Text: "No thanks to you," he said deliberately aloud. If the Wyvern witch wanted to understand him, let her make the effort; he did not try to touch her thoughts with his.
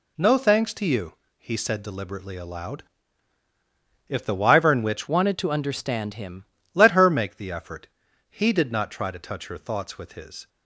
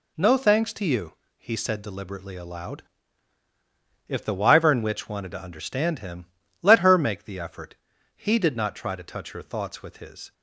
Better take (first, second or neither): second